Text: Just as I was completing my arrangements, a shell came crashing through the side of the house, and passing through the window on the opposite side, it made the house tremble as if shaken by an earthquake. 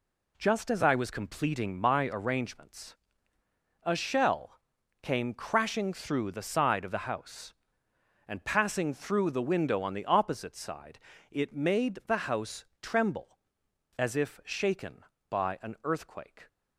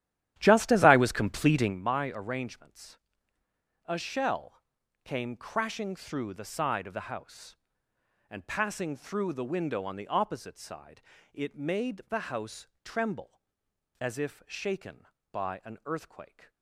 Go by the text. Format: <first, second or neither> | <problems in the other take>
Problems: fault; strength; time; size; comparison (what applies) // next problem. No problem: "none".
first | starts louder than the rest; strong; until 1.8 s; 12 dB // pauses between "shell" and "came"; at 4.6 s; 0.42 s long; also in the first // pauses between "house" and "tremble"; slight; at 12.6 s; 0.18 s long; slight in the first